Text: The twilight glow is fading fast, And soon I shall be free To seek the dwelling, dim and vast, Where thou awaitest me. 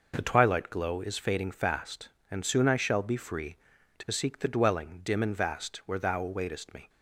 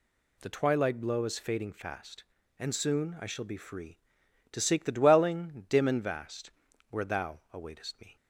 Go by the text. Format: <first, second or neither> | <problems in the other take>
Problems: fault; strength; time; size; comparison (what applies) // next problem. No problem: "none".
first | says "blow" for "glow"; at 0.9 s